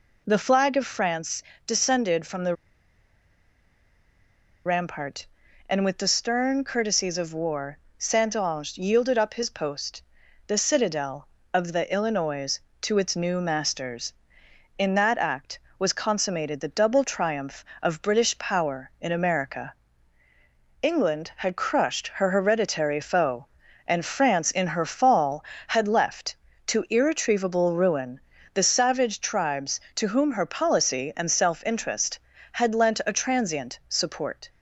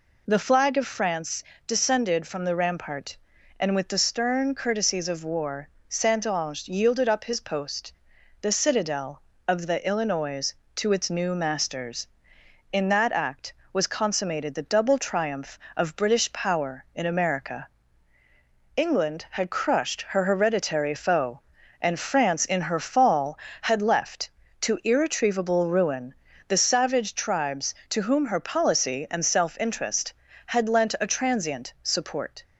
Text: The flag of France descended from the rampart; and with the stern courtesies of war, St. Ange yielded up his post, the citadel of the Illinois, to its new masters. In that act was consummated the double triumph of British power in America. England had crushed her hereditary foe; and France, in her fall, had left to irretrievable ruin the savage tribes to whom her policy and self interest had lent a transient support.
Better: second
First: pauses between "France" and "descended"; slight; at 1.4 s; 0.24 s long // pauses between "the" and "rampart"; strong; at 2.5 s; 2.1 s long // pauses between "ruin" and "the"; slight; at 28.1 s; 0.36 s long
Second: pauses between "France" and "descended"; slight; at 1.4 s; 0.24 s long // pauses between "ruin" and "the"; slight; at 26.1 s; 0.36 s long

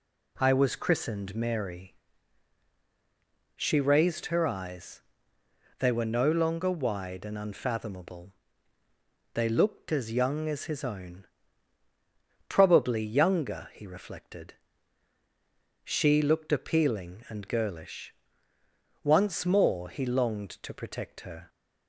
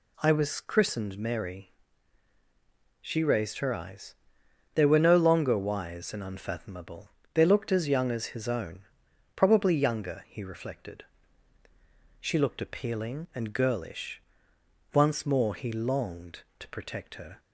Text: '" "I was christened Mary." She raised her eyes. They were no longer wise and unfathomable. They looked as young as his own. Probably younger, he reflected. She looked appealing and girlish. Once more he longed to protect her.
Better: second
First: says "wide" for "wise"; at 6.6 s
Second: none

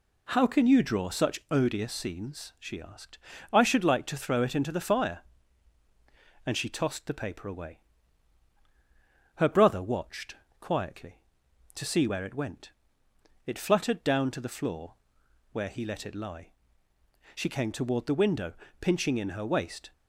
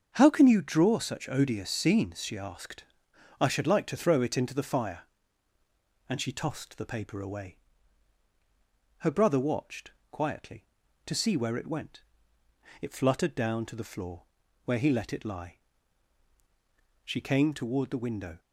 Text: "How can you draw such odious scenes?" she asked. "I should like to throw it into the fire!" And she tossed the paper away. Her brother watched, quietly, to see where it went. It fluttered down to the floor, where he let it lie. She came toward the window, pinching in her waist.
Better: first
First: none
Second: starts louder than the rest; until 1.1 s; 6.5 dB // stops before "pinching in her waist"; at 18.3 s

